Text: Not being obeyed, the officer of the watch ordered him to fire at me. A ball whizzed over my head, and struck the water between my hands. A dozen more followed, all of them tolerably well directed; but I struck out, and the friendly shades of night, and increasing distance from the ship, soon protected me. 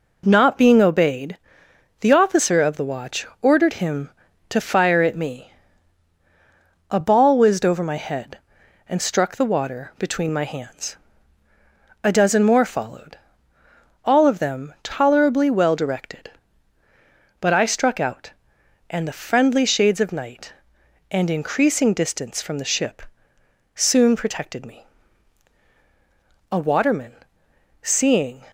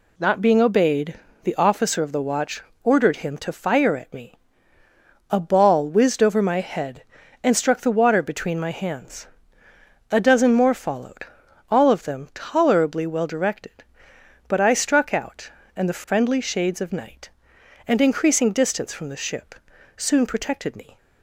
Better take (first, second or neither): second